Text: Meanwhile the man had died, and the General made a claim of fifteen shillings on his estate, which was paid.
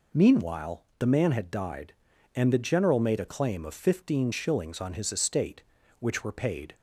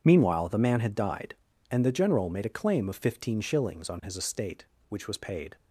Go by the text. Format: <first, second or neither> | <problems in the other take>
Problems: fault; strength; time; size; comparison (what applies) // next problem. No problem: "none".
second | says "were" for "was"; at 6.2 s